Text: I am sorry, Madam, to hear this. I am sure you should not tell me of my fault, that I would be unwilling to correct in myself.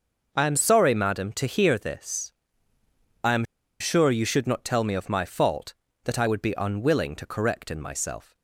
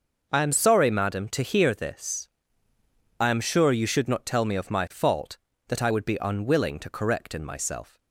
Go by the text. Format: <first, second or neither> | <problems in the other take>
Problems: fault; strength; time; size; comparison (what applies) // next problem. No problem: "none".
second | pauses between "am" and "sure"; at 3.4 s; 0.36 s long